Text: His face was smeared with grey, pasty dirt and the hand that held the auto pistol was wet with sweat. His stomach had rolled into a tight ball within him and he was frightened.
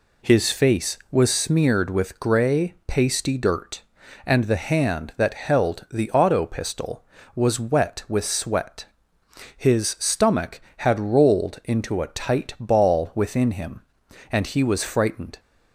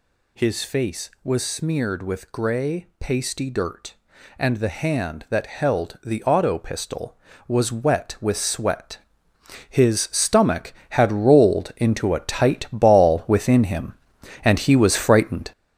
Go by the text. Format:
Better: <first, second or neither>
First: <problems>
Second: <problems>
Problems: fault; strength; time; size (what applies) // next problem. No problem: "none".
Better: first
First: none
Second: gets louder; throughout; 7 dB